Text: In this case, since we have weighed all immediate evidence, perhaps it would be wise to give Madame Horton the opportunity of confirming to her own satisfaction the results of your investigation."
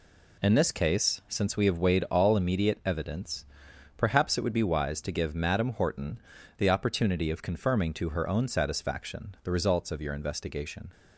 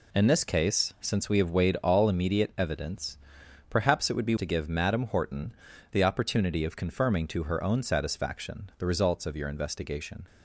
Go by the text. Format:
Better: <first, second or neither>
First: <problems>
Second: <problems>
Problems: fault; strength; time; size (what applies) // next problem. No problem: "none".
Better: first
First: pauses between "Horton" and "the"; at 6.1 s; 0.38 s long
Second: skips "wise"; at 4.3 s // pauses between "Horton" and "the"; at 5.5 s; 0.38 s long